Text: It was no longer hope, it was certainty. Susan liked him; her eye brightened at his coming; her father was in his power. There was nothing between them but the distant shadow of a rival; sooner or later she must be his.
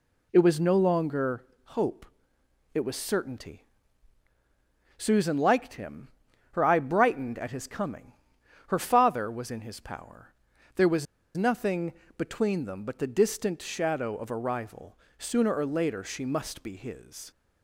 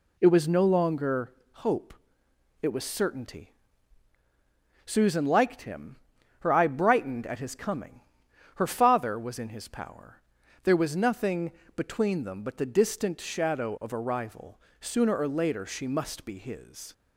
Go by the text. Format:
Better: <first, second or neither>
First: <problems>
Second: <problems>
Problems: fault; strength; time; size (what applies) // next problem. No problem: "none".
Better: second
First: pauses between "longer" and "hope"; slight; at 1.4 s; 0.20 s long // pauses between "was" and "nothing"; slight; at 11.0 s; 0.31 s long // pauses between "nothing" and "between"; slight; at 11.9 s; 0.24 s long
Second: pauses between "longer" and "hope"; slight; at 1.3 s; 0.20 s long // pauses between "nothing" and "between"; slight; at 11.5 s; 0.24 s long